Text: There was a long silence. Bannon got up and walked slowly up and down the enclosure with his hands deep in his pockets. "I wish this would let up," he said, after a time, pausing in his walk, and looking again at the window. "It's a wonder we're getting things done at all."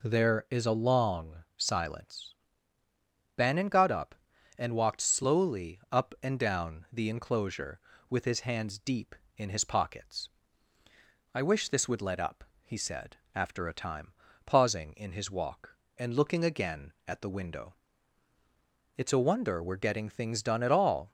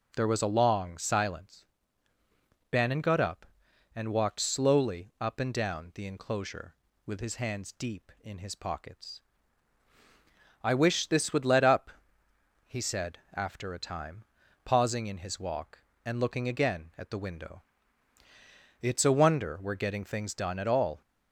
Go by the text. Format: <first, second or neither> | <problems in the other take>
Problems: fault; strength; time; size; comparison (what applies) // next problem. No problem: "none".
second | says "is" for "was"; at 0.4 s